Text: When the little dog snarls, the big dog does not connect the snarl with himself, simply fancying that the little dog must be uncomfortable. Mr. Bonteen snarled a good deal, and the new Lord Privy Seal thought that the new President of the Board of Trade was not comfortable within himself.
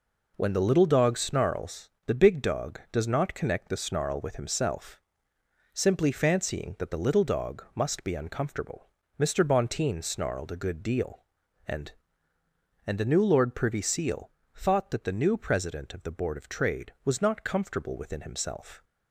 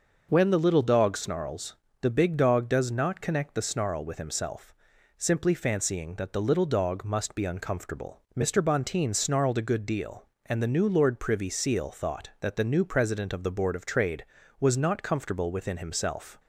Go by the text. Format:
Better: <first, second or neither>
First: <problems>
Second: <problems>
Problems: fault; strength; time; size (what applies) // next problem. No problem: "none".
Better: second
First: says "and" twice; at 12.8 s // pauses between "Seal" and "thought"; slight; at 14.3 s; 0.24 s long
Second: none